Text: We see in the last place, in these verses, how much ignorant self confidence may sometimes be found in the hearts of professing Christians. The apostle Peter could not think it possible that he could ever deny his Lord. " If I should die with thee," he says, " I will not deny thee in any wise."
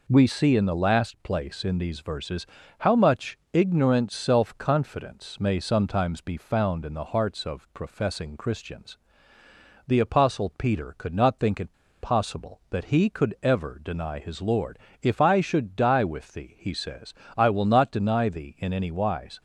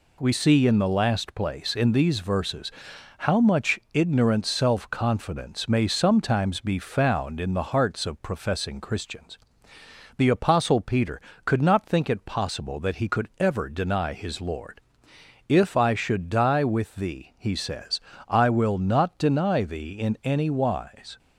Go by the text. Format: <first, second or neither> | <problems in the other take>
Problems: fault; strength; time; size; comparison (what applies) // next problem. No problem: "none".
second | pauses between "it" and "possible"; slight; at 11.7 s; 0.29 s long